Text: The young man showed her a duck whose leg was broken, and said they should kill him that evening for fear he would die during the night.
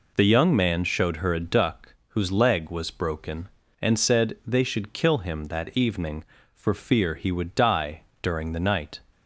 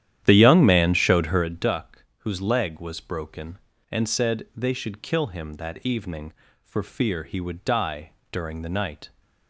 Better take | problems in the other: first | starts louder than the rest; strong; until 1.5 s; 11 dB // pauses between "die" and "during"; slight; at 8.1 s; 0.18 s long; slight in the first

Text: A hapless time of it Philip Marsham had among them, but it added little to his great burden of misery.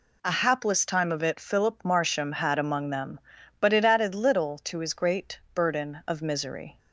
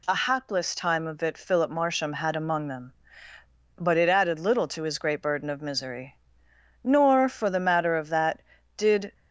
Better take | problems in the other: first | goes on to say "Nor for the matter of that did"; strong; from 6.8 s on; 2.3 s long

